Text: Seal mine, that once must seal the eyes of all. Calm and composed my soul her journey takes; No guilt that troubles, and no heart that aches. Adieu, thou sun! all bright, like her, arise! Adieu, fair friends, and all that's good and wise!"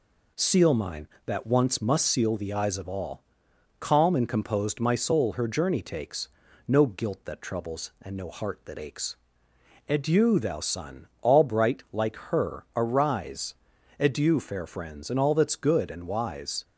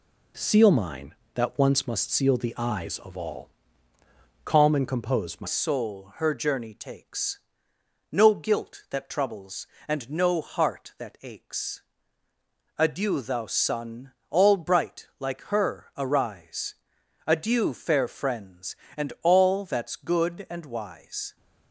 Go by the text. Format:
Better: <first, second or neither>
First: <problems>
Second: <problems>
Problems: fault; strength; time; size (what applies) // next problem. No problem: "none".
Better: first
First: none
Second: changes voice at "soul"; from 5.4 s on; 15.9 s long